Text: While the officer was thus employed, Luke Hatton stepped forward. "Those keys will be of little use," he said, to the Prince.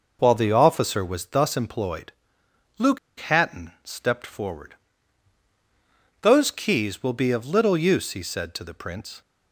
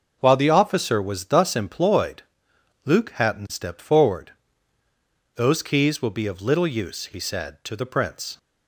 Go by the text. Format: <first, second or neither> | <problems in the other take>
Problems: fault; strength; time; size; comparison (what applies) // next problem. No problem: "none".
second | pauses between "Luke" and "Hatton"; slight; at 2.9 s; 0.20 s long